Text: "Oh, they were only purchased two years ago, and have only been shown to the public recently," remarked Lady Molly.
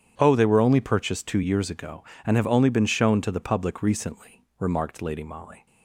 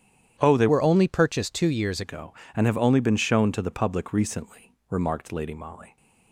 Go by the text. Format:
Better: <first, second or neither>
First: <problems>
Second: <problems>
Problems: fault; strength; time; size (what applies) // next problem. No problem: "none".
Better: first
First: starts louder than the rest; strong; until 1.1 s; 9 dB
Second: starts louder than the rest; strong; until 1.4 s; 10 dB // changes voice from "were" to "years"; from 0.6 to 2.0 s; 1.4 s long